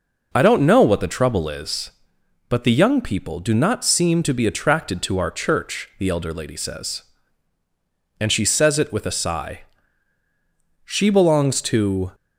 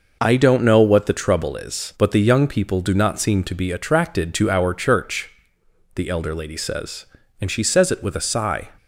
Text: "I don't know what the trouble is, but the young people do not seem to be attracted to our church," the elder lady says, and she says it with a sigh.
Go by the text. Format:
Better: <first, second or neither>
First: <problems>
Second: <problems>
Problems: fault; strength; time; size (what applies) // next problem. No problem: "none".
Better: second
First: goes on to say "She belongs to"; noticeable; from 10.8 s on; 1.2 s long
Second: none